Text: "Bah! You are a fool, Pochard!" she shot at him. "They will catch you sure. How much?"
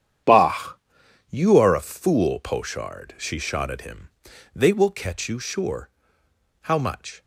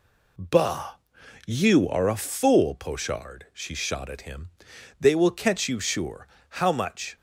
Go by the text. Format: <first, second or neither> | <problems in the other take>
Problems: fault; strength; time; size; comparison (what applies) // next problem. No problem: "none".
second | gets quieter; strong; throughout; 13 dB